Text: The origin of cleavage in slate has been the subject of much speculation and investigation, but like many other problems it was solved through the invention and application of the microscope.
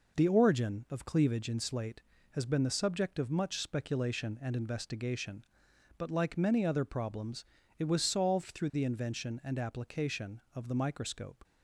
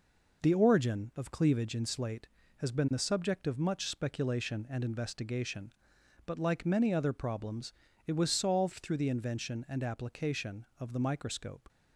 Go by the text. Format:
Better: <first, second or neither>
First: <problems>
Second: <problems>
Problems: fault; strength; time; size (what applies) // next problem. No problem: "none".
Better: neither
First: pauses between "problems" and "it"; slight; at 7.4 s; 0.36 s long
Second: pauses between "problems" and "it"; slight; at 7.7 s; 0.36 s long